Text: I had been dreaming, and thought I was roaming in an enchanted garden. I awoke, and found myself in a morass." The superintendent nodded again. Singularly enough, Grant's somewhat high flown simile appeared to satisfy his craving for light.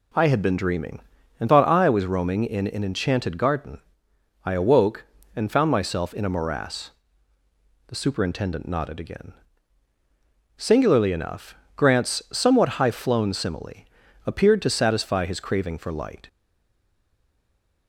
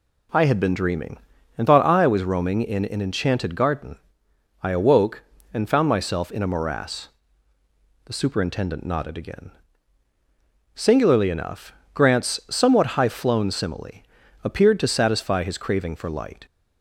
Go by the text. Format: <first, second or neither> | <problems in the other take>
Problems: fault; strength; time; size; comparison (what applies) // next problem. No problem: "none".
second | pauses between "simile" and "appeared"; at 13.8 s; 0.40 s long; also in the second // stays silent after the last word; noticeable; from 16.2 s on; 1.6 s long